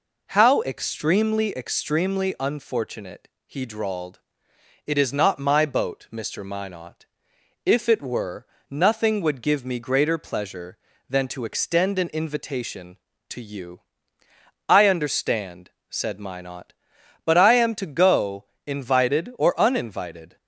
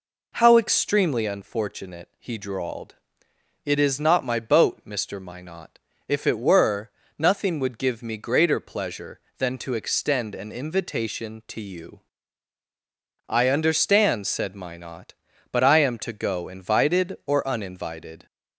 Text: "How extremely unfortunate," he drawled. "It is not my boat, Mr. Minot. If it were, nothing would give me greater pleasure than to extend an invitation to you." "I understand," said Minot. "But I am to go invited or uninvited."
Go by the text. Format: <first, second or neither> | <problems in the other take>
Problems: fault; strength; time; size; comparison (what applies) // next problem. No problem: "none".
second | says "extremely" twice; at 1.5 s // pauses between "go" and "invited"; slight; at 18.4 s; 0.18 s long